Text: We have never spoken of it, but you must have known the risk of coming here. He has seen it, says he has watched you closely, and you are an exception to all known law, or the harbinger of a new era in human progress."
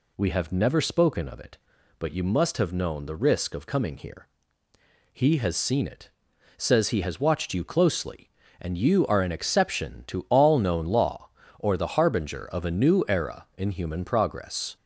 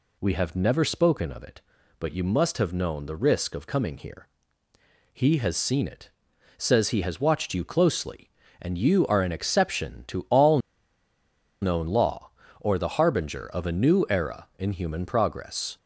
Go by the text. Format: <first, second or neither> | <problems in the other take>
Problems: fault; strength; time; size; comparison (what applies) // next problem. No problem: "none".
first | pauses between "all" and "known"; at 10.5 s; 1.0 s long